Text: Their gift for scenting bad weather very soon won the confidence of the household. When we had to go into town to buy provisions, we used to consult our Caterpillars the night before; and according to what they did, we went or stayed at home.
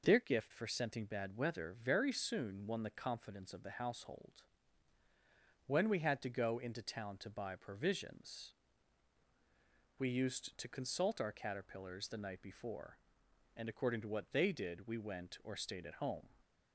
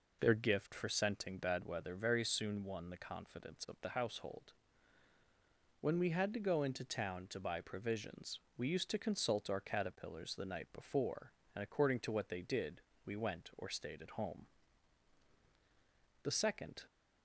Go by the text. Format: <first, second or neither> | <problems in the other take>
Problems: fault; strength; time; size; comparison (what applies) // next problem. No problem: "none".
first | goes on to say "The second"; noticeable; from 16.2 s on; 0.62 s long